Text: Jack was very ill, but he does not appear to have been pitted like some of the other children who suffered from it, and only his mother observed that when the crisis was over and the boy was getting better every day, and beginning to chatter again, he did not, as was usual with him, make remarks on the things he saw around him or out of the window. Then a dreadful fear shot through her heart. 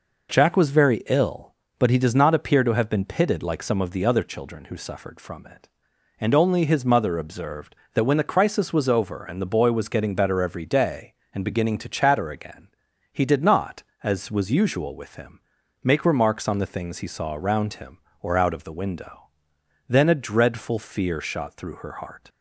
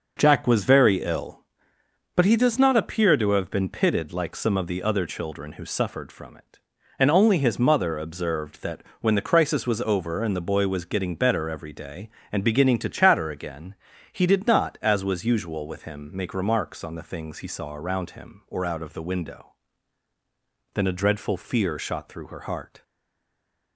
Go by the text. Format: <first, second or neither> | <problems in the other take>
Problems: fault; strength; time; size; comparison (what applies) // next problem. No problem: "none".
first | pauses between "that" and "when"; slight; at 8.8 s; 0.18 s long // stays silent after the last word; slight; from 22.8 s on; 0.9 s long